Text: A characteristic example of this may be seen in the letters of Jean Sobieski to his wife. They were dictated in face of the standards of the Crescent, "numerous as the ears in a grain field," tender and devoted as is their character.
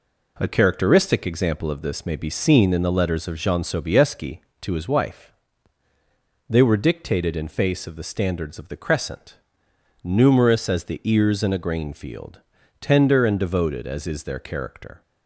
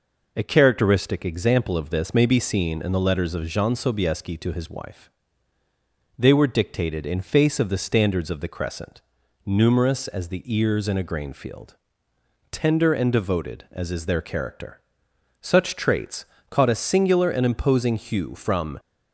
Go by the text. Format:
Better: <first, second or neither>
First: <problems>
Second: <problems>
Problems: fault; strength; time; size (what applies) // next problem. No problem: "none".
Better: first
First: none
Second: goes on to say "Such traits caught a singular and imposing hue from"; strong; from 15.3 s on; 3.4 s long